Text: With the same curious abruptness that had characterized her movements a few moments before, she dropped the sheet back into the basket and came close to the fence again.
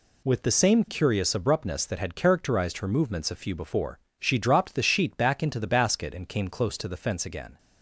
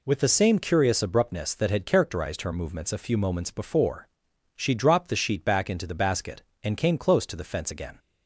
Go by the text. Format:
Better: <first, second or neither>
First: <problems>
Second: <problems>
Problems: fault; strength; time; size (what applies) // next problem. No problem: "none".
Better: second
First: skips "moments"; at 3.5 s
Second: none